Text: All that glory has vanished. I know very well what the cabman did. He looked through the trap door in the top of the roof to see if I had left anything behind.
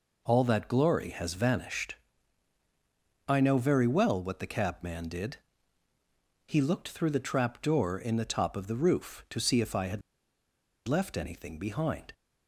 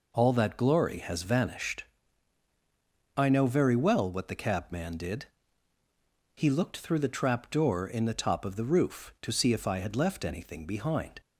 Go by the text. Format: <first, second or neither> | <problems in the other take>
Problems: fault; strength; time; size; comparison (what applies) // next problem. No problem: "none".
second | pauses between "had" and "left"; noticeable; at 10.0 s; 0.86 s long